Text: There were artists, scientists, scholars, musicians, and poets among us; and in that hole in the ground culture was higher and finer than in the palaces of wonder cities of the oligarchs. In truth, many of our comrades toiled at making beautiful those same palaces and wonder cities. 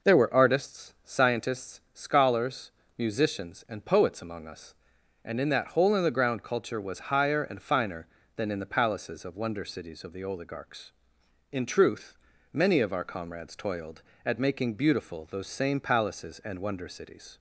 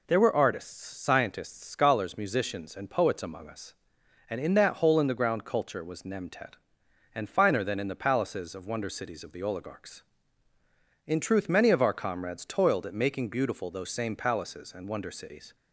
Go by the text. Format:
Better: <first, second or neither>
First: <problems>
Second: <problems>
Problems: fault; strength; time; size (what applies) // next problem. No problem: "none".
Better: first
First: none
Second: says "nemtet" for "higher"; at 6.0 s